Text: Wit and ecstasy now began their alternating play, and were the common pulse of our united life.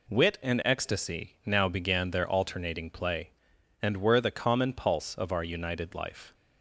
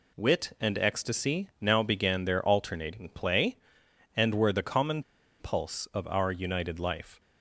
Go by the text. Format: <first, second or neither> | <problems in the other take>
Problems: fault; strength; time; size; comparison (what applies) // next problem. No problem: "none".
first | pauses between "common" and "pulse"; at 5.0 s; 0.38 s long